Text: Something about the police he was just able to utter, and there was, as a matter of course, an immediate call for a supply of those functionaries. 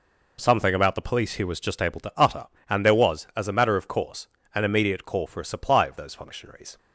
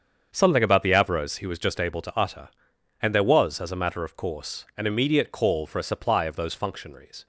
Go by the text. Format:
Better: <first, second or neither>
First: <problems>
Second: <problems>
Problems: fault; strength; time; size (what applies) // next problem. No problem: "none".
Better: first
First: none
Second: starts louder than the rest; strong; until 1.3 s; 7.5 dB // says "avros" for "police"; at 0.9 s